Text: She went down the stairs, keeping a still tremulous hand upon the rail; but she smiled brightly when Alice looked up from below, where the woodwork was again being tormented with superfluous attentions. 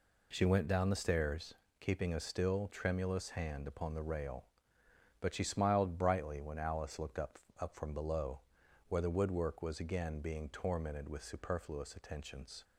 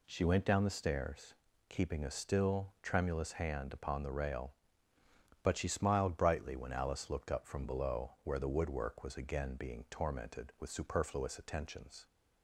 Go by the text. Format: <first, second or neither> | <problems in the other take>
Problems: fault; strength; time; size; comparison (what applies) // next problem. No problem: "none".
second | says "up" twice; at 7.5 s